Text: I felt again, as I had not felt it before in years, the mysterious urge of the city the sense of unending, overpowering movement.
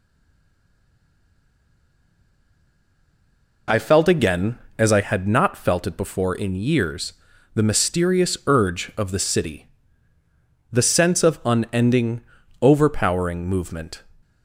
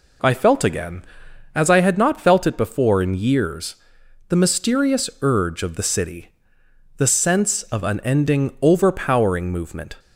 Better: second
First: stays silent before the first word; strong; until 3.6 s; 3.6 s long // pauses between "city" and "the"; at 9.6 s; 1.0 s long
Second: pauses between "city" and "the"; noticeable; at 6.2 s; 0.68 s long

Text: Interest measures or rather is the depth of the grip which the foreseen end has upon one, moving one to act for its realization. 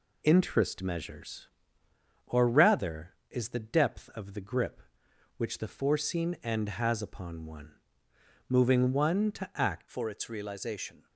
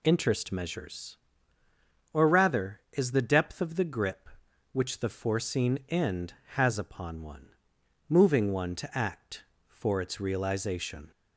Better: second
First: changes voice at "for"; from 9.8 s on; 1.2 s long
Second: none

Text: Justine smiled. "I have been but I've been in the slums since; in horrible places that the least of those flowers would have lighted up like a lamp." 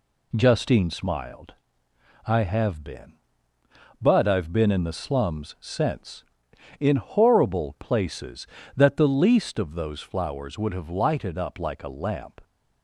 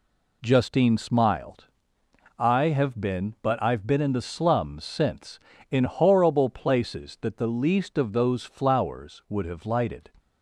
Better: first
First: none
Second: stops before "up like a lamp"; at 10.1 s

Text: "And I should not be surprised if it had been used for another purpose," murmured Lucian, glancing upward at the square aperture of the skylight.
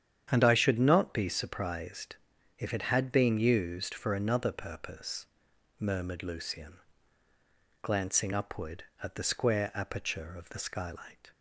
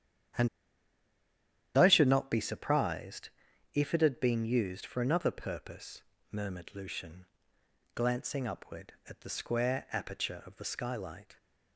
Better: first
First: starts louder than the rest; strong; until 1.3 s; 9 dB // pauses between "surprised" and "if"; at 2.1 s; 0.42 s long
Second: starts louder than the rest; strong; until 2.6 s; 9.5 dB // pauses between "And" and "I"; strong; at 0.4 s; 1.2 s long // pauses between "surprised" and "if"; at 3.2 s; 0.44 s long

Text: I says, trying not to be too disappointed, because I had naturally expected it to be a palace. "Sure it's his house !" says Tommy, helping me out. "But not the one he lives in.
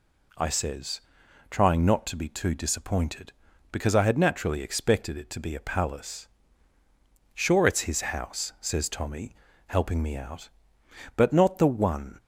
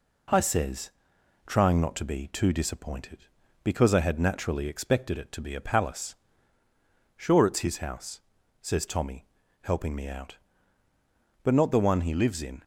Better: second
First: stops before "he lives in"; at 12.1 s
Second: none

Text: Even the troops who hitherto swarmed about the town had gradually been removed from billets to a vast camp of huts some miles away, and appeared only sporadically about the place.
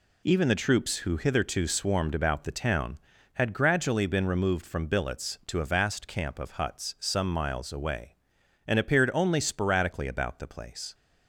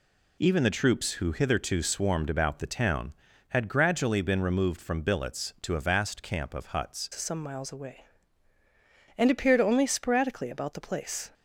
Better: first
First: none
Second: changes voice at "some"; from 7.1 s on; 4.2 s long

